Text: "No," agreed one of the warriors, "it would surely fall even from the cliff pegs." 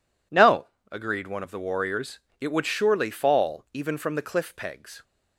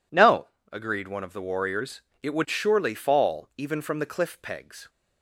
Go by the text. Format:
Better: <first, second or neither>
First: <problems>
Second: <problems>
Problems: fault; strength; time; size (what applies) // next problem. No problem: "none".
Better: neither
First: none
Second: none